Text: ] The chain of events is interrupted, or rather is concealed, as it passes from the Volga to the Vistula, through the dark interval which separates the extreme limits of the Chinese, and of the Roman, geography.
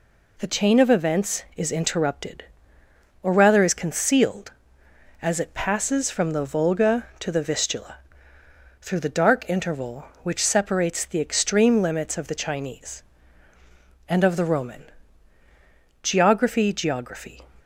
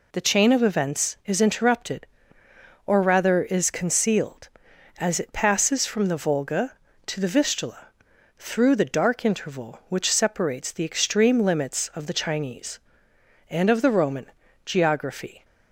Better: second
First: says "geography" twice; at 16.7 s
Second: none

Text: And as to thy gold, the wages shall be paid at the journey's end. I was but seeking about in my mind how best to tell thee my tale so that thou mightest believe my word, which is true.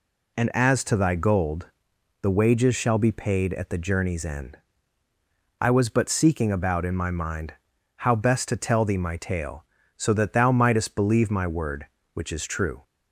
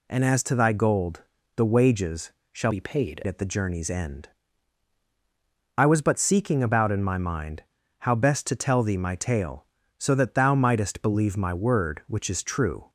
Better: first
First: pauses between "mind" and "how"; at 7.5 s; 0.44 s long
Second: pauses between "wages" and "shall"; slight; at 2.3 s; 0.20 s long // changes voice from "be" to "paid"; from 2.7 to 3.2 s; 0.5 s long // pauses between "mind" and "how"; at 7.6 s; 0.38 s long

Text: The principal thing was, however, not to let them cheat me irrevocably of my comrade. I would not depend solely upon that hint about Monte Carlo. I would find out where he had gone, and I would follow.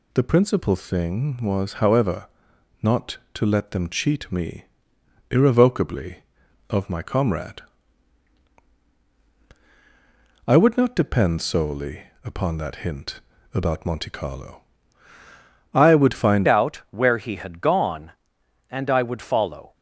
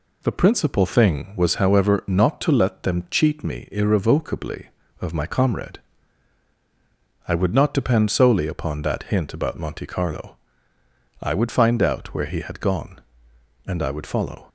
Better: second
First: pauses between "me" and "irrevocably"; noticeable; at 4.6 s; 0.64 s long // pauses between "solely" and "upon"; slight; at 12.0 s; 0.24 s long // pauses between "hint" and "about"; slight; at 13.2 s; 0.32 s long // changes voice at "out"; from 16.4 s on; 3.3 s long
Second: none

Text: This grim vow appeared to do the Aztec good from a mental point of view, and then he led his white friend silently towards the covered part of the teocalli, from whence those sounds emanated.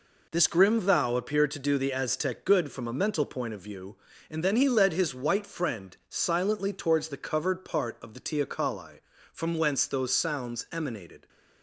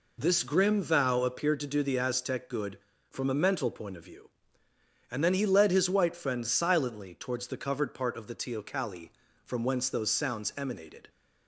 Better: neither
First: none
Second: none

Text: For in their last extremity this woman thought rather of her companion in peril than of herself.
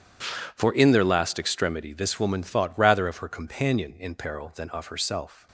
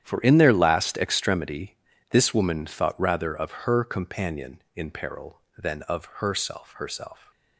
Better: first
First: starts louder than the rest; strong; until 1.2 s; 9 dB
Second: starts louder than the rest; strong; until 1.0 s; 10 dB // pauses between "extremity" and "this"; slight; at 1.7 s; 0.34 s long // says "herself" twice; at 6.7 s

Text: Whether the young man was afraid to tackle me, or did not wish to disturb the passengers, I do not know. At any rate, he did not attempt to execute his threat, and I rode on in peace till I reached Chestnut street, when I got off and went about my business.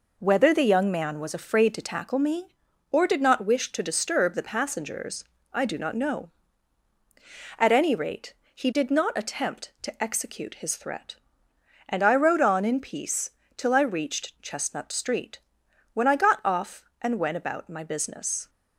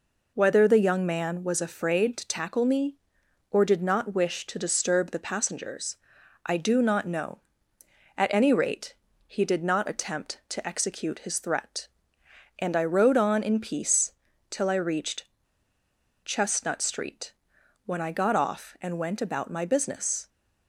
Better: first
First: pauses between "peace" and "till"; slight; at 13.2 s; 0.26 s long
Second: pauses between "peace" and "till"; slight; at 14.1 s; 0.36 s long // pauses between "reached" and "Chestnut"; at 15.2 s; 0.98 s long

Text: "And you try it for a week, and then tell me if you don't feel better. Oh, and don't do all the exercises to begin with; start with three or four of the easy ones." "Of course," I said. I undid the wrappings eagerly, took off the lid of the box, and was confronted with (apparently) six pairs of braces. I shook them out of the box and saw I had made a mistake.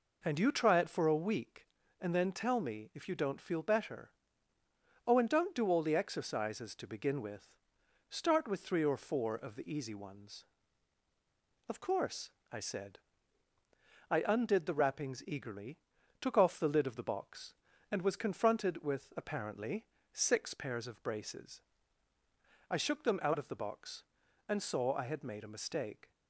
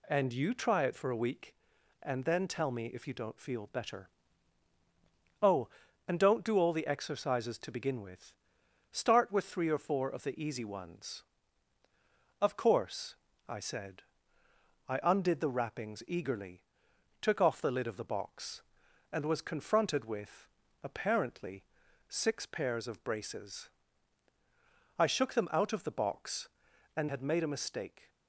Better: first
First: none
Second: skips "saw I"; at 27.0 s

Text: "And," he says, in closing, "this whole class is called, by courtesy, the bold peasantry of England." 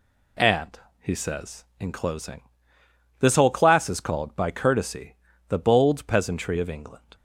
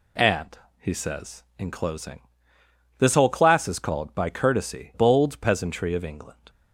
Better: first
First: none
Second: skips "the"; at 4.9 s

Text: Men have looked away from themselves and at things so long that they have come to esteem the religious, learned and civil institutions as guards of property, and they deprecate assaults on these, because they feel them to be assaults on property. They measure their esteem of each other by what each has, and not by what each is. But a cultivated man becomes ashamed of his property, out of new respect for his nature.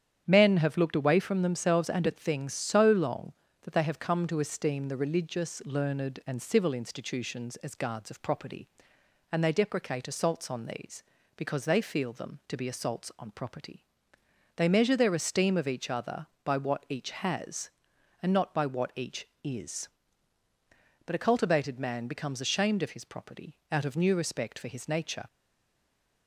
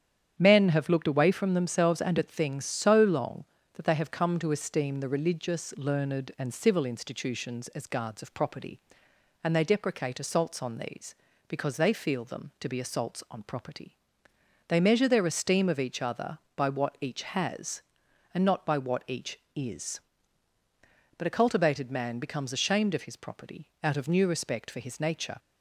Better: second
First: starts louder than the rest; strong; until 1.2 s; 9.5 dB // stays silent after the last word; from 25.2 s on; 1.0 s long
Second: starts louder than the rest; strong; until 1.3 s; 9.5 dB

